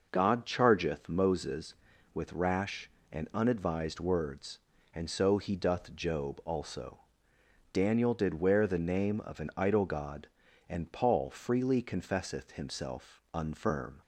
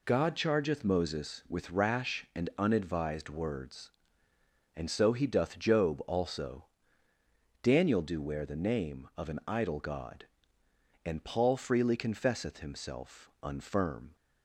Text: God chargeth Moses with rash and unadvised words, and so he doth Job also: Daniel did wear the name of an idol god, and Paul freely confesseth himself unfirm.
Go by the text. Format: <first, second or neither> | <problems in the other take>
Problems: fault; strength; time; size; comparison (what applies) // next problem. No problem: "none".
first | says "do" for "did"; at 8.0 s